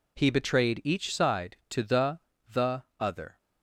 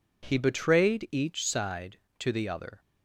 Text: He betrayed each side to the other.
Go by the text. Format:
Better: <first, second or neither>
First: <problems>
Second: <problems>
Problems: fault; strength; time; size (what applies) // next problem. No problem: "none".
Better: second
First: says "the" twice; at 2.4 s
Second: none